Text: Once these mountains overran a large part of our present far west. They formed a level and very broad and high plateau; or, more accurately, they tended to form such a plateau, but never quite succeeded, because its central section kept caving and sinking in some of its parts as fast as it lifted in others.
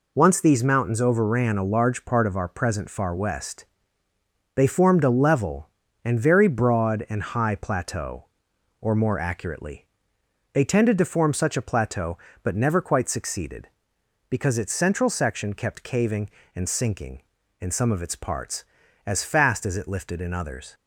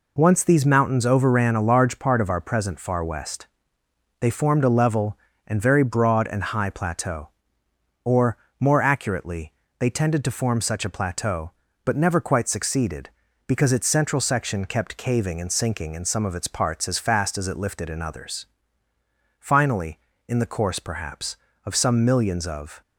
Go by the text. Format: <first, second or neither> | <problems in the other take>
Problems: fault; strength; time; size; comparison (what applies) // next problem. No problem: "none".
first | goes on to say "Finally in the course perhaps of some millions of"; strong; from 19.3 s on; 3.4 s long